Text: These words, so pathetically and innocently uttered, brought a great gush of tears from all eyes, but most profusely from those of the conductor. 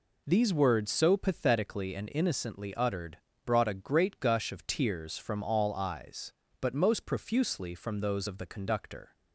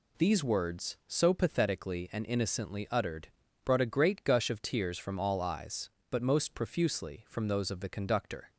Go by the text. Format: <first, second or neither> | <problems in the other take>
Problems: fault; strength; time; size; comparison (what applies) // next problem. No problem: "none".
neither | none